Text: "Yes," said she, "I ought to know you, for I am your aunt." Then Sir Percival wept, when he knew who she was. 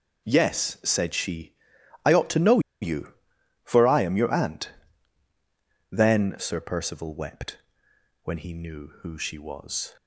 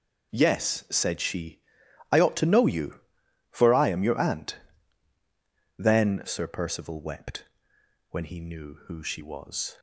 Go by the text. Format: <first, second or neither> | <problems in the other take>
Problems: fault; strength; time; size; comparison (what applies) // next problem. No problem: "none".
second | pauses between "know" and "you"; slight; at 2.5 s; 0.22 s long